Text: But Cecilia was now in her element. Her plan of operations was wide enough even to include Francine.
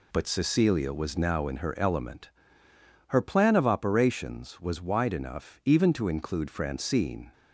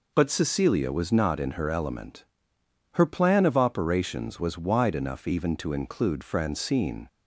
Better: first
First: none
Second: says "not" for "now"; at 1.1 s

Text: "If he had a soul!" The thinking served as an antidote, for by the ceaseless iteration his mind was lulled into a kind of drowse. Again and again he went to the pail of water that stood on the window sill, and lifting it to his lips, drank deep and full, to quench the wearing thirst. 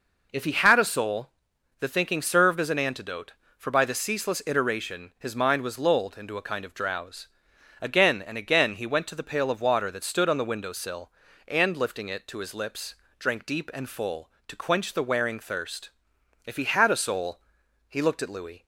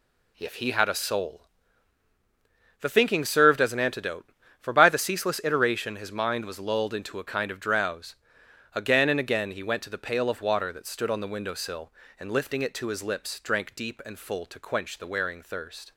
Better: second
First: goes on to say "If he had a soul He looked at Louis"; strong; from 16.4 s on; 2.2 s long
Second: none

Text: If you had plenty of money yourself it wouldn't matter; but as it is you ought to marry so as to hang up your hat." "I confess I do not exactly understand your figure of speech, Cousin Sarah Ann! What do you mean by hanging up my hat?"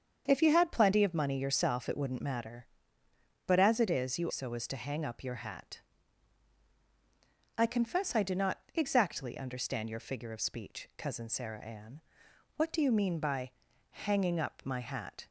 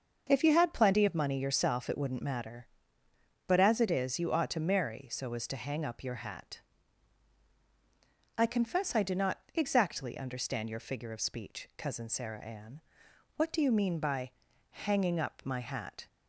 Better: second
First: starts louder than the rest; strong; until 1.2 s; 7.5 dB // skips "ought to marry"; at 4.3 s // pauses between "not" and "exactly"; slight; at 8.5 s; 0.16 s long // pauses between "by" and "hanging"; at 13.5 s; 0.38 s long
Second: starts louder than the rest; until 1.3 s; 6.5 dB // pauses between "not" and "exactly"; slight; at 9.3 s; 0.16 s long // pauses between "by" and "hanging"; at 14.3 s; 0.38 s long

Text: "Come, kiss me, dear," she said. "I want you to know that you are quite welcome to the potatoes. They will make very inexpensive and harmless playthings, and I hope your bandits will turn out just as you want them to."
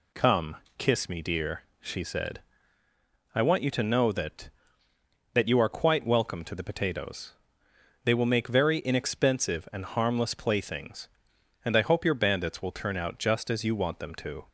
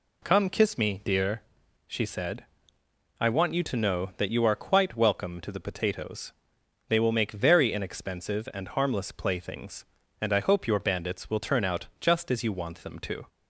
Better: second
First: says "that" twice; at 5.3 s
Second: none

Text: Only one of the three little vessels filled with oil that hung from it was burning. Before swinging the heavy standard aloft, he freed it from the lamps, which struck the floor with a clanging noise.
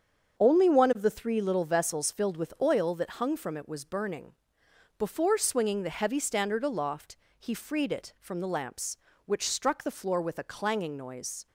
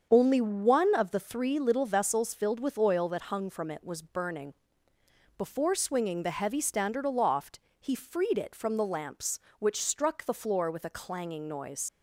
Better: first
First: starts louder than the rest; until 1.4 s; 7 dB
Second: starts louder than the rest; until 1.1 s; 7 dB // leaves "noise" unfinished; at 11.8 s; 60 ms

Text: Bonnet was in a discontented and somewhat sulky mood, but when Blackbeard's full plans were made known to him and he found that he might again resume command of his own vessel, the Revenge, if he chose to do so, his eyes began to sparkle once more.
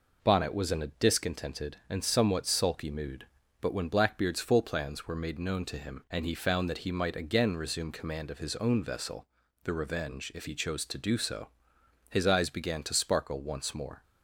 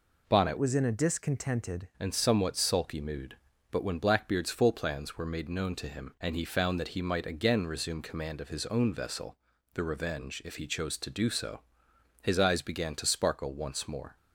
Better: first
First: none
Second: changes voice from "was" to "discontented"; from 0.5 to 1.8 s; 1.3 s long

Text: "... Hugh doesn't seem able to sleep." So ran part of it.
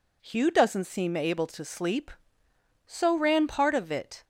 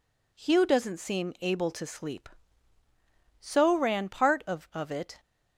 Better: first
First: none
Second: says "of" twice; at 4.7 s

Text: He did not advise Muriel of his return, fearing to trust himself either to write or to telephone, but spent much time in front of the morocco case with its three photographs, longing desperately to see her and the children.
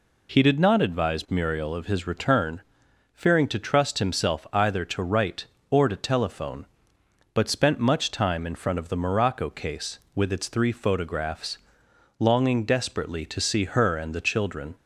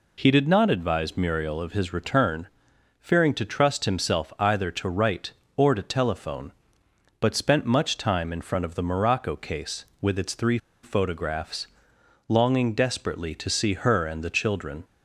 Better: first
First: none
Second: pauses between "three" and "photographs"; slight; at 10.5 s; 0.24 s long

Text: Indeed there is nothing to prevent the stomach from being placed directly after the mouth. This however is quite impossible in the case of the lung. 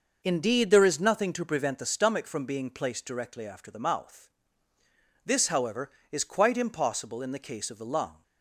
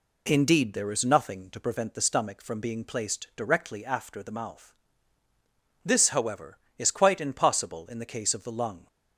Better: neither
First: none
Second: none

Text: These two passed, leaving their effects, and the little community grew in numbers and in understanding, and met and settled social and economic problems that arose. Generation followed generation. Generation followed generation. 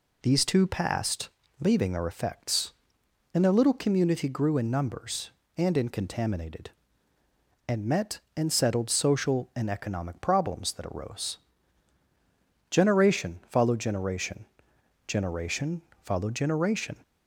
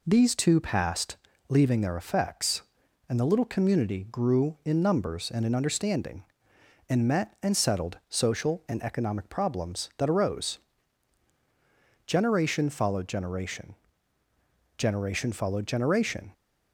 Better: second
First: says "contaminated" for "understanding"; at 5.8 s // pauses between "Generation" and "followed"; slight; at 15.8 s; 0.22 s long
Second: none

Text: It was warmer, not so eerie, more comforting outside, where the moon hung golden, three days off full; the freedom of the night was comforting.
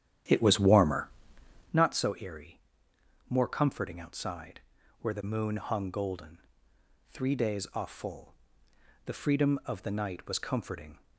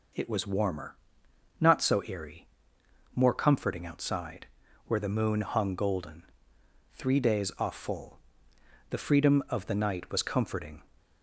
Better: second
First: starts louder than the rest; strong; until 1.8 s; 10.5 dB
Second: none

